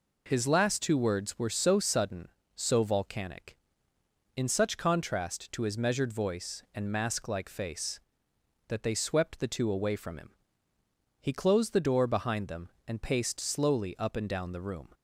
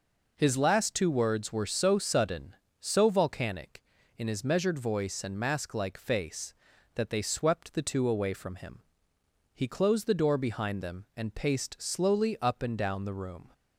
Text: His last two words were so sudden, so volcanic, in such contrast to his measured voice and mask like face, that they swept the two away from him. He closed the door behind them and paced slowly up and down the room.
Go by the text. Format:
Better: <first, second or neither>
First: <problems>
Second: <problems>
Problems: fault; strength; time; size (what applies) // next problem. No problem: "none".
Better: first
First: none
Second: skips "such contrast to"; at 4.2 s